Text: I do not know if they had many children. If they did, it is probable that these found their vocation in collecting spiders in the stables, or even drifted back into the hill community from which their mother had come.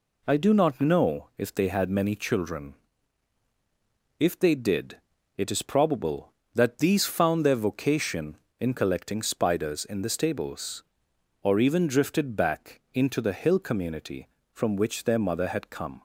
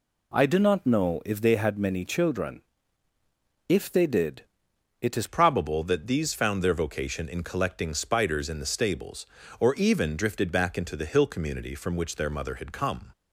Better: first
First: none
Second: changes voice at "probable"; from 5.2 s on; 7.9 s long

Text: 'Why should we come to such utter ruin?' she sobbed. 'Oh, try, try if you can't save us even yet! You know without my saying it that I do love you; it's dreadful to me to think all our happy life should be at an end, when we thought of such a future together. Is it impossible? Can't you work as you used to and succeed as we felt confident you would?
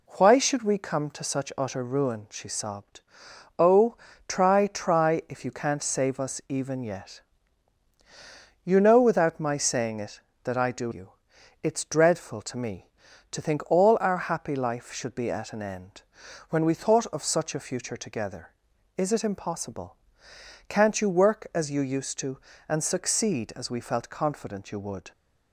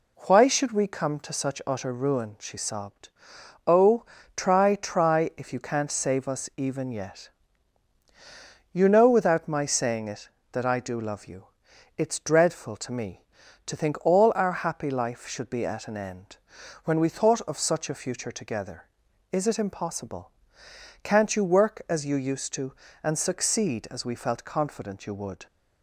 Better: second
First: skips "love"; at 10.9 s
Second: none

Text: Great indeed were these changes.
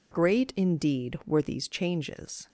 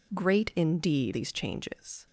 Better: first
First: none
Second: skips "were"; at 1.1 s

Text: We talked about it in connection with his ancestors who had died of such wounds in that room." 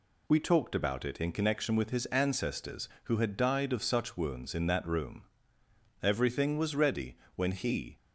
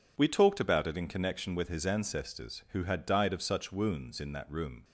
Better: second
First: goes on to say "Everything was ready when he"; strong; from 6.0 s on; 1.9 s long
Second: none

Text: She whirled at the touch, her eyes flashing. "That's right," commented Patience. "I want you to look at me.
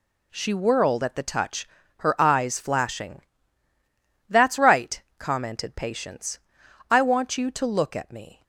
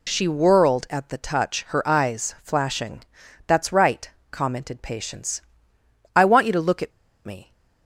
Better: first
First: none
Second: pauses between "at" and "me"; slight; at 6.9 s; 0.36 s long

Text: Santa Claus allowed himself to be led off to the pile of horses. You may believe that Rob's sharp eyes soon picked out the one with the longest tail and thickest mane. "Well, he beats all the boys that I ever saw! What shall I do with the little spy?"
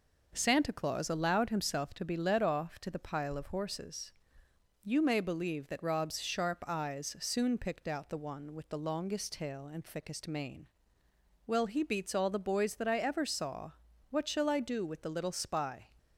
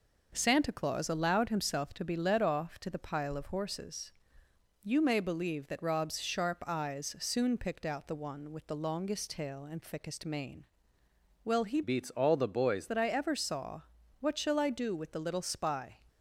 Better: first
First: none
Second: changes voice from "beats" to "boys"; from 11.8 to 12.8 s; 1.0 s long

